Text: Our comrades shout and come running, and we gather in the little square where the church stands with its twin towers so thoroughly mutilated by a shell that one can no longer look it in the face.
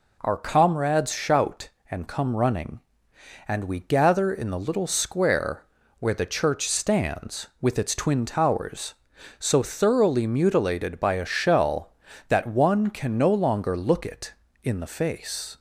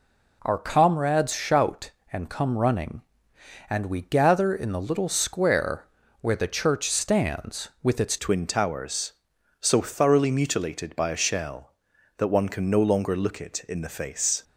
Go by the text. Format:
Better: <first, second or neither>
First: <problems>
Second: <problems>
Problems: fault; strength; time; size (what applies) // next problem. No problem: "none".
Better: first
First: pauses between "square" and "where"; at 5.6 s; 0.38 s long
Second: pauses between "square" and "where"; at 5.8 s; 0.38 s long // changes voice at "twin"; from 8.1 s on; 6.3 s long